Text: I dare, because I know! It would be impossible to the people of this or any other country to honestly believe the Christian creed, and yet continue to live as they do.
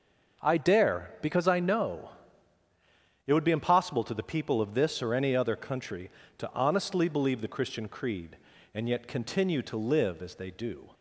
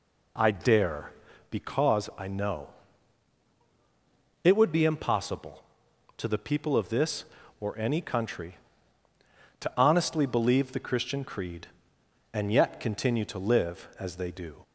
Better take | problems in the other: first | skips "other"; at 8.0 s

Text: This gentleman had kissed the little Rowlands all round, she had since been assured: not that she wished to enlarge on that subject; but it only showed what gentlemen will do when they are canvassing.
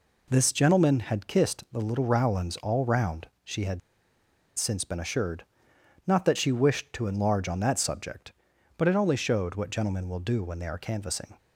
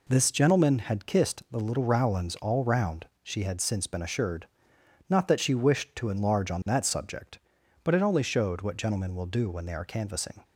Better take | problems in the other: second | pauses between "had" and "since"; noticeable; at 3.7 s; 0.77 s long

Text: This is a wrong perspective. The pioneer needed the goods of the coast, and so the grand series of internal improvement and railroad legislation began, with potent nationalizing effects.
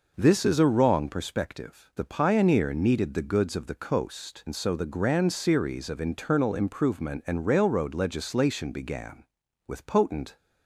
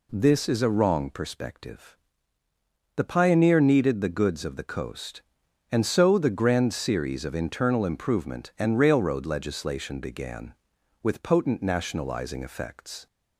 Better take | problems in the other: second | stops before "nationalizing effects"; at 10.3 s

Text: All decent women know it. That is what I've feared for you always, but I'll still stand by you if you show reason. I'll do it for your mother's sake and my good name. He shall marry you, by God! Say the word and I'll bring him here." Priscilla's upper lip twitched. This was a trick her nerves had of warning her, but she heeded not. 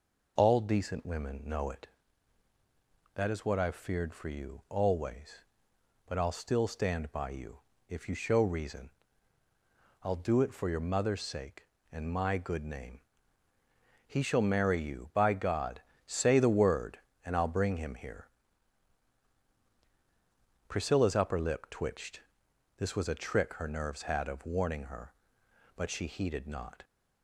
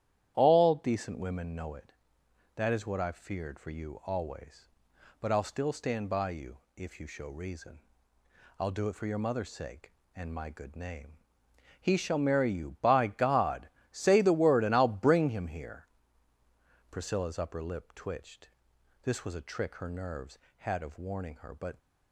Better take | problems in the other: first | starts louder than the rest; strong; until 1.3 s; 11 dB // pauses between "you" and "if"; slight; at 6.5 s; 0.18 s long; slight in the first // stops before "she heeded not"; at 21.7 s

